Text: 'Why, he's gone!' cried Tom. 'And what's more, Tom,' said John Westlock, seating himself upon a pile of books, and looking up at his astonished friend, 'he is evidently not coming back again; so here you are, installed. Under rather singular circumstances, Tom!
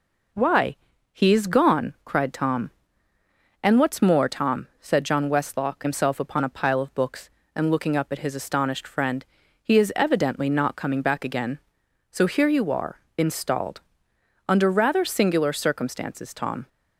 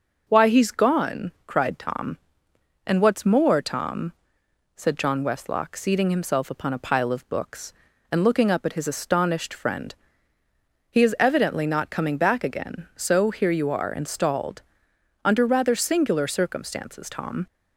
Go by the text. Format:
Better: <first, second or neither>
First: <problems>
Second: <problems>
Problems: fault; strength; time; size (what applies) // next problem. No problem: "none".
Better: second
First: skips "seating"; at 5.8 s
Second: none